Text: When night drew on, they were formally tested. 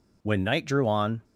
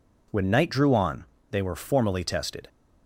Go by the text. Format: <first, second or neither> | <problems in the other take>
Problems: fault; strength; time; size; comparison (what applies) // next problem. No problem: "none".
second | stops before "they were formally tested"; at 1.2 s